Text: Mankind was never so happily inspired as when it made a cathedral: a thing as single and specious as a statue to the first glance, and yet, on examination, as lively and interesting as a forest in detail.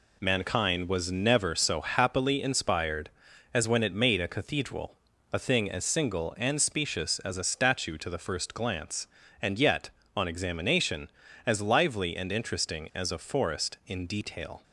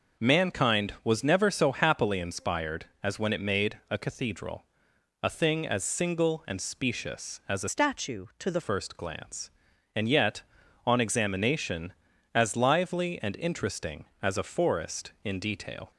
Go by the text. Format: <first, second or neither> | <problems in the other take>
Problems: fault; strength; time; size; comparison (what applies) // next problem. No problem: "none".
first | changes voice from "statue" to "the"; from 7.6 to 8.6 s; 1.0 s long